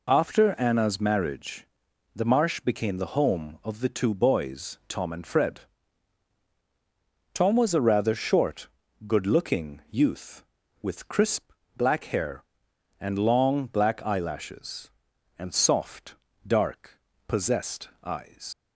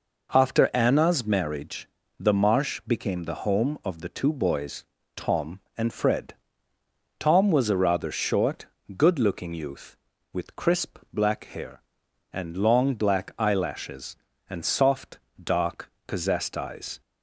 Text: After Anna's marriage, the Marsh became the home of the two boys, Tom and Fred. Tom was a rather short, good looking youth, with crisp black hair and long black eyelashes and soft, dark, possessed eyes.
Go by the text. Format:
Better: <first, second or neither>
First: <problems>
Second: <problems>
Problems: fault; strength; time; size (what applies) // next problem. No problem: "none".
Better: second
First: pauses between "crisp" and "black"; slight; at 11.5 s; 0.26 s long // leaves "eyes" unfinished; at 18.5 s; 100 ms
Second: none